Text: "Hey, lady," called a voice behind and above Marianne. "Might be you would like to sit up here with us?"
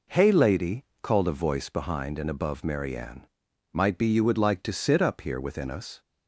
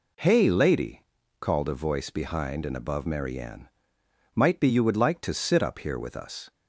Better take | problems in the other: second | says "within" for "with"; at 5.4 s

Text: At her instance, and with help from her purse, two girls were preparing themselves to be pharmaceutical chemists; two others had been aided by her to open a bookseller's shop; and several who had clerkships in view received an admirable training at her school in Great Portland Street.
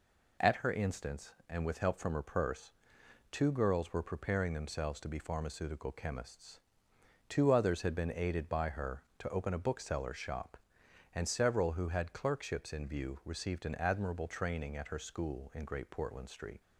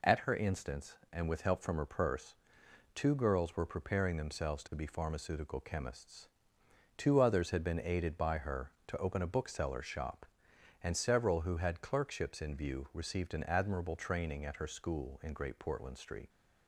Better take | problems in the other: neither | none

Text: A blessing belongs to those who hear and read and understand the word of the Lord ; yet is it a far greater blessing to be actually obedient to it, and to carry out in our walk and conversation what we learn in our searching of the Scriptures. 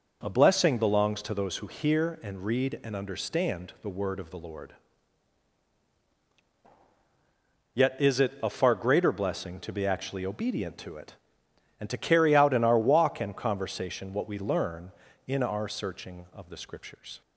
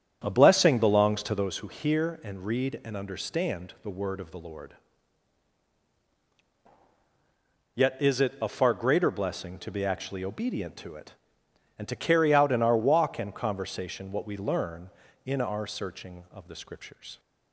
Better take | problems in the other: first | starts louder than the rest; strong; until 1.5 s; 8.5 dB

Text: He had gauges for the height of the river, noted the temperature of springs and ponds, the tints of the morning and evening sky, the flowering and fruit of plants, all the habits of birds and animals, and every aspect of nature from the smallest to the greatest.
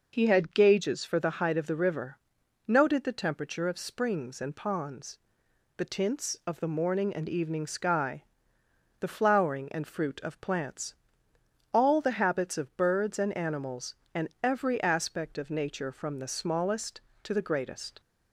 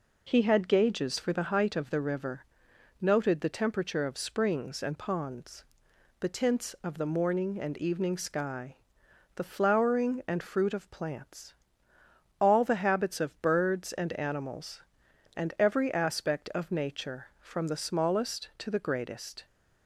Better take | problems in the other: neither | none

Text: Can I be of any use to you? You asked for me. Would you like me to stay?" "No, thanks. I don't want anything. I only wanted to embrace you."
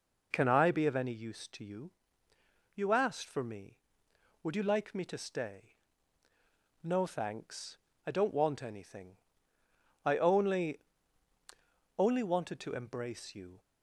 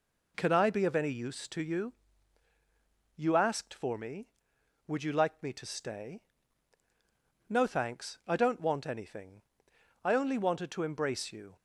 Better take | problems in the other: second | says "only" twice; at 11.9 s

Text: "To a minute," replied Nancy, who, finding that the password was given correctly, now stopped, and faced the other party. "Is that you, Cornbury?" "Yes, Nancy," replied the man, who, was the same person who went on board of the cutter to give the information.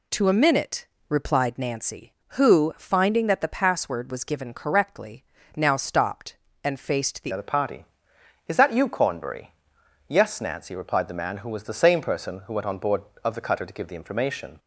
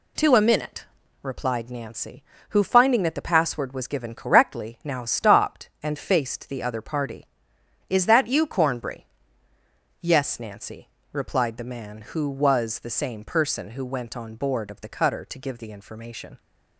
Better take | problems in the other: second | changes voice at "other"; from 7.3 s on; 7.2 s long

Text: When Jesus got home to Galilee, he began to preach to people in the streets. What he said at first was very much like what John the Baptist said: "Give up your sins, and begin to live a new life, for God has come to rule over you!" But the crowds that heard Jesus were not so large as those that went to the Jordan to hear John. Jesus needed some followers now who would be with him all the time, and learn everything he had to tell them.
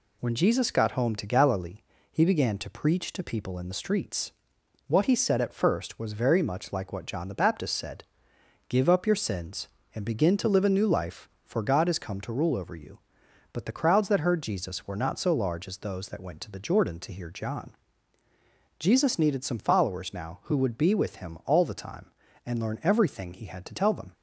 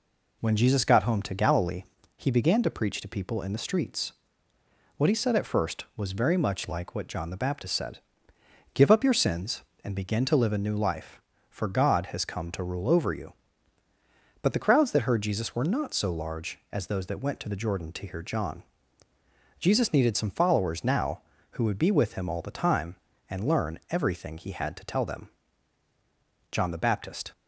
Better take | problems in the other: first | goes on to say "John the Baptist"; noticeable; from 26.5 s on; 0.80 s long

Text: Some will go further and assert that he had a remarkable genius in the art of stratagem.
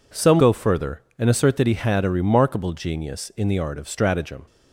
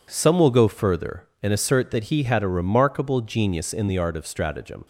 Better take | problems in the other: second | skips "will"; at 0.3 s

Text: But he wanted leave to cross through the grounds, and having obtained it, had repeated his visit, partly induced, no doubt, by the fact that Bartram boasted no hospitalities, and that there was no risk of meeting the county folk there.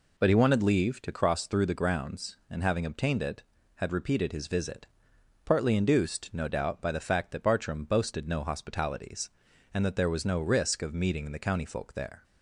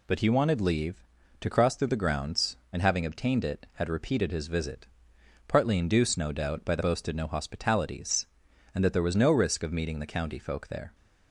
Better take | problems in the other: first | skips "fact that Bartram"; at 6.8 s

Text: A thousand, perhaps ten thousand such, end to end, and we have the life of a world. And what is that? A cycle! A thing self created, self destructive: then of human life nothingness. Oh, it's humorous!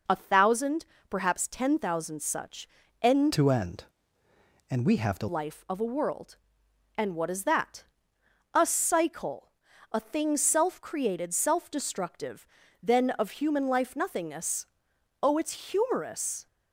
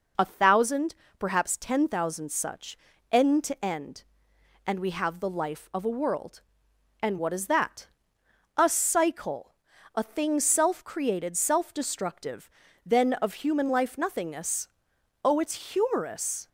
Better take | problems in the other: second | changes voice from "to" to "the"; from 3.3 to 5.2 s; 1.9 s long

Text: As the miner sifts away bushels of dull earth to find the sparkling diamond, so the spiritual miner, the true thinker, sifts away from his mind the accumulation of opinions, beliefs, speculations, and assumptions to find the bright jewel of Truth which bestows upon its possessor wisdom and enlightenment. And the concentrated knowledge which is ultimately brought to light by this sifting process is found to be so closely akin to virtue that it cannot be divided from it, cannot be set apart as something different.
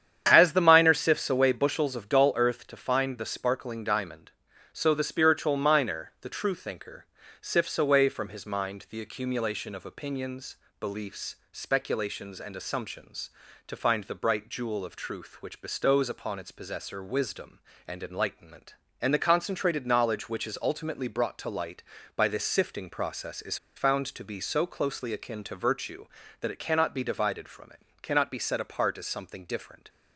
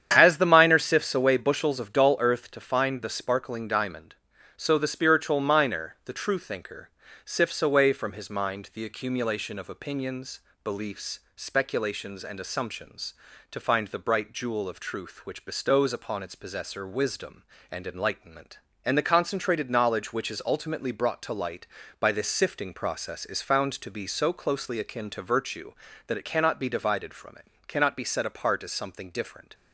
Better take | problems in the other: second | starts louder than the rest; strong; until 1.2 s; 9 dB; strong in the second // pauses between "is" and "found"; slight; at 23.5 s; 0.19 s long

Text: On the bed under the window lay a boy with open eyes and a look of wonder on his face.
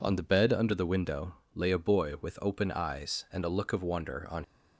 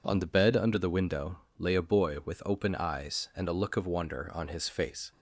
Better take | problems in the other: second | pauses between "window" and "lay"; slight; at 1.3 s; 0.18 s long; slight in the second // stops before "his face"; at 4.4 s

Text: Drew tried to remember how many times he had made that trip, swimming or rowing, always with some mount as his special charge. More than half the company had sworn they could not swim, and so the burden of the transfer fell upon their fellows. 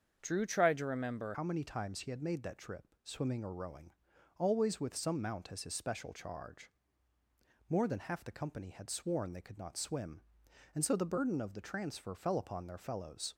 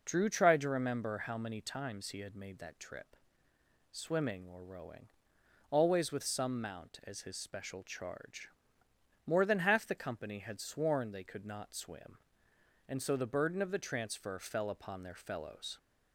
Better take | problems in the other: second | starts louder than the rest; until 1.2 s; 7 dB // changes voice at "how"; from 1.3 s on; 12.0 s long

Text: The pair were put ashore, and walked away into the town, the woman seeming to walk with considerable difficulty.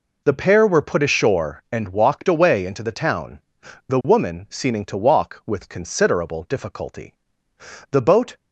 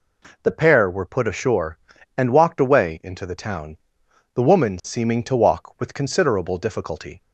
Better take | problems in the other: second | goes on to say "The boat"; slight; from 7.9 s on; 0.44 s long

